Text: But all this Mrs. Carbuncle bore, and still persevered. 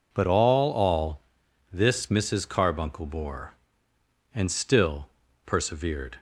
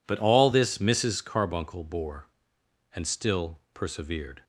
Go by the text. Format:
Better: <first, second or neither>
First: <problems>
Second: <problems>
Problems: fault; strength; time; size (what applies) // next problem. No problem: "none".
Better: second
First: says "all" twice; at 0.7 s // pauses between "still" and "persevered"; slight; at 5.0 s; 0.36 s long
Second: none